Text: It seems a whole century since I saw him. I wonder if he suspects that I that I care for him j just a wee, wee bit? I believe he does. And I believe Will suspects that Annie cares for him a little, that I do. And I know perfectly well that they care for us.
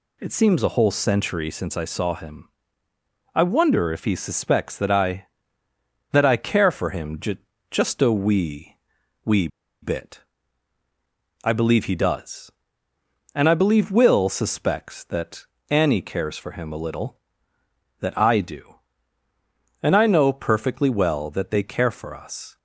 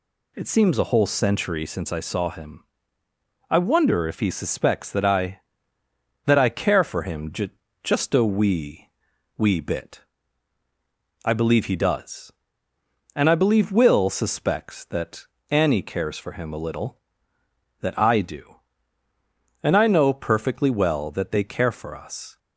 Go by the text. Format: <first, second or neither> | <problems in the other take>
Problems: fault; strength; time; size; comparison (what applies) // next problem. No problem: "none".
second | pauses between "j" and "just"; slight; at 7.3 s; 0.34 s long; slight in the second // pauses between "wee" and "bit"; slight; at 9.4 s; 0.34 s long // pauses between "that" and "Annie"; slight; at 15.4 s; 0.24 s long; slight in the second